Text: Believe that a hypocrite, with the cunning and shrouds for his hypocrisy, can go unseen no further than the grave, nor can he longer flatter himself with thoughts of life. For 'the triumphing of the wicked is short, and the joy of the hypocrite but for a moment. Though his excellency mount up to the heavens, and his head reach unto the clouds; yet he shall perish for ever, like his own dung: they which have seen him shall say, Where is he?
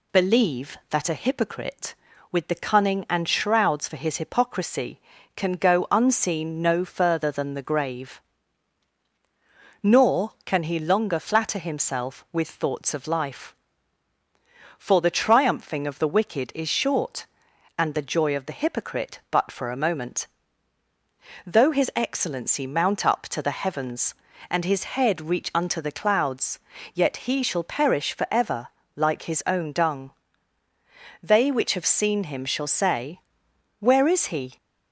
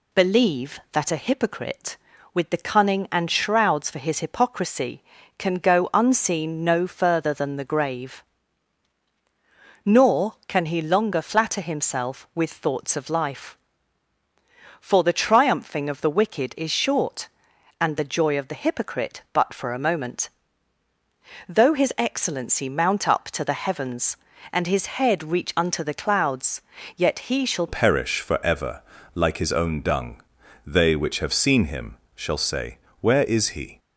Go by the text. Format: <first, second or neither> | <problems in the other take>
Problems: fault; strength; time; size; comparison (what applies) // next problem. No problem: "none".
first | changes voice at "perish"; from 27.6 s on; 6.1 s long // pauses between "him" and "shall"; slight; at 31.9 s; 0.22 s long